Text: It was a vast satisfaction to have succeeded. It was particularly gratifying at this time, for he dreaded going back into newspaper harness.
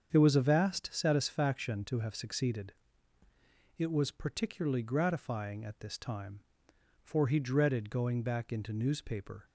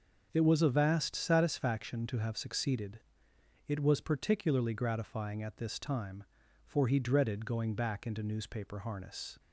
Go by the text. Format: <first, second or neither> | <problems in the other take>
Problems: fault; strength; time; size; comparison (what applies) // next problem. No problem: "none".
second | starts louder than the rest; strong; until 1.1 s; 7.5 dB; also in the second // stops before "harness"; at 9.4 s